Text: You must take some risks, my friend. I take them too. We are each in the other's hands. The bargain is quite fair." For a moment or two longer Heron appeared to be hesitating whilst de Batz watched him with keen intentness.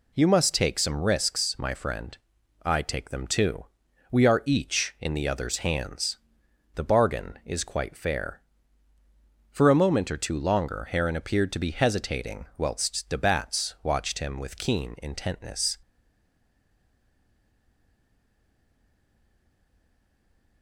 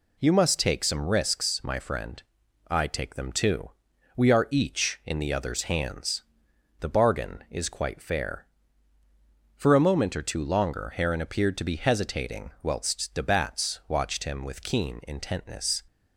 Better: second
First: stays silent after the last word; strong; from 15.8 s on; 4.8 s long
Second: none

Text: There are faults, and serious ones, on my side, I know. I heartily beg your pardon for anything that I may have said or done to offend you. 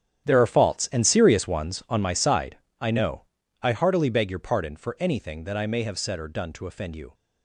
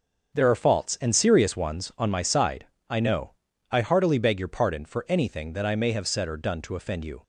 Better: second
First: gets quieter; strong; throughout; 14 dB // starts louder than the rest; strong; until 1.3 s; 9.5 dB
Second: starts louder than the rest; until 1.3 s; 6.5 dB

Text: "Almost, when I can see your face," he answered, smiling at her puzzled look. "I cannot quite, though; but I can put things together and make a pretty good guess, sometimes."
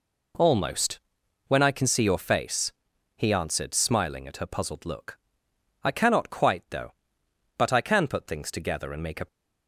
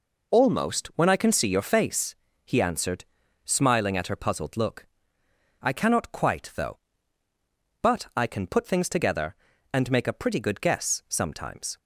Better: second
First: stops before "pretty good guess sometimes"; at 9.2 s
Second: none

